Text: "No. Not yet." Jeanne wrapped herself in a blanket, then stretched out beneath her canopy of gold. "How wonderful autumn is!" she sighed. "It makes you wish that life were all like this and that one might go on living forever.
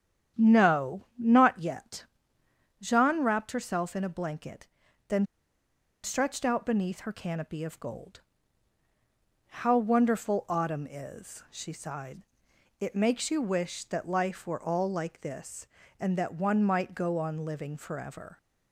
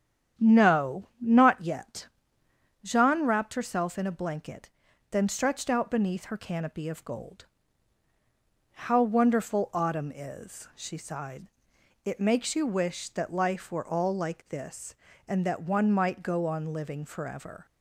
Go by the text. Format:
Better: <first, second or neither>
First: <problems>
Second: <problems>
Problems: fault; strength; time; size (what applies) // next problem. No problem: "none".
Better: second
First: starts louder than the rest; strong; until 1.4 s; 9 dB // pauses between "then" and "stretched"; noticeable; at 5.2 s; 0.79 s long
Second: starts louder than the rest; strong; until 1.4 s; 8.5 dB